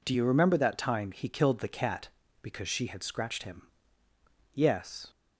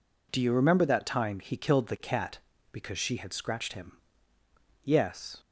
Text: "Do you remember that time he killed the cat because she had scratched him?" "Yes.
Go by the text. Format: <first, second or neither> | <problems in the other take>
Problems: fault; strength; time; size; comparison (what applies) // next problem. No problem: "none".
neither | none